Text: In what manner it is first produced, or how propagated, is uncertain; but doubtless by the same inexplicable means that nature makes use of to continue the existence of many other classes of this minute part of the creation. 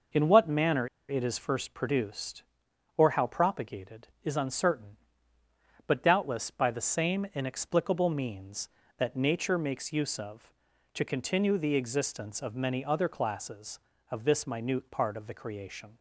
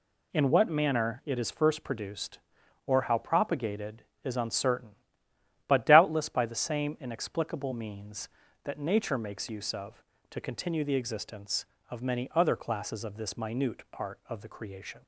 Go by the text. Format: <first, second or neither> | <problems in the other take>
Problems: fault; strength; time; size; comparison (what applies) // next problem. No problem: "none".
second | pauses between "manner" and "it"; slight; at 0.8 s; 0.23 s long